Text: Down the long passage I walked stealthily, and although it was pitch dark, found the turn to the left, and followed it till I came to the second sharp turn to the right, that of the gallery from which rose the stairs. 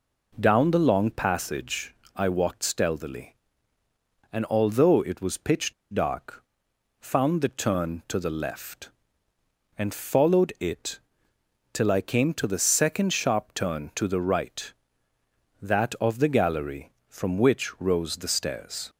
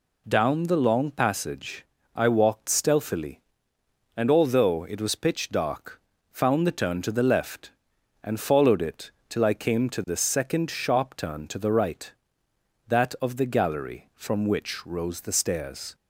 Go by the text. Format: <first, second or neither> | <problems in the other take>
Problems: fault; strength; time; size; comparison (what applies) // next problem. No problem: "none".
second | pauses between "passage" and "I"; slight; at 1.9 s; 0.22 s long; slight in the second // pauses between "pitch" and "dark"; slight; at 5.7 s; 0.20 s long // pauses between "it" and "till"; noticeable; at 10.9 s; 0.74 s long; slight in the second